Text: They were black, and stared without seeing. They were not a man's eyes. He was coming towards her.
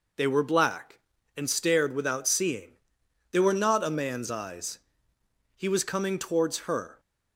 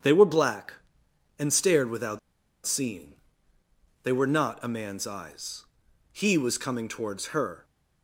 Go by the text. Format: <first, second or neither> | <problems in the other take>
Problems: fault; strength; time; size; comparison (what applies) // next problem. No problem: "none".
first | starts louder than the rest; strong; until 1.6 s; 7.5 dB // pauses between "without" and "seeing"; noticeable; at 2.1 s; 0.47 s long